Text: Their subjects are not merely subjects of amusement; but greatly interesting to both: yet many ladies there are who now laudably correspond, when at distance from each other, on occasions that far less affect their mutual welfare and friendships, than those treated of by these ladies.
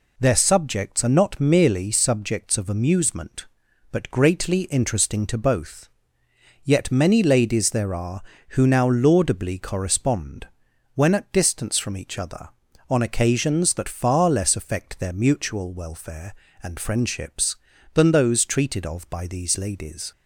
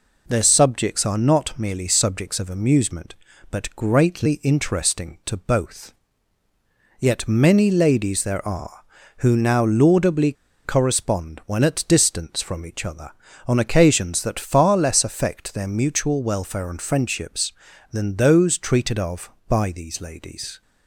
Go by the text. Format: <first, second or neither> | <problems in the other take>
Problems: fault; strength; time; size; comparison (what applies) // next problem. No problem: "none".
first | pauses between "laudably" and "correspond"; slight; at 10.3 s; 0.31 s long